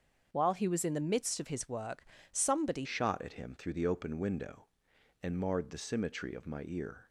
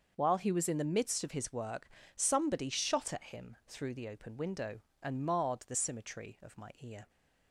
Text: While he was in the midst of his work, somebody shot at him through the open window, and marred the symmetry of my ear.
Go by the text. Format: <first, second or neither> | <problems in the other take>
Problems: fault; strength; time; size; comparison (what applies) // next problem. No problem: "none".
second | starts louder than the rest; until 1.3 s; 7 dB; also in the second // changes voice at "shot"; from 2.8 s on; 4.2 s long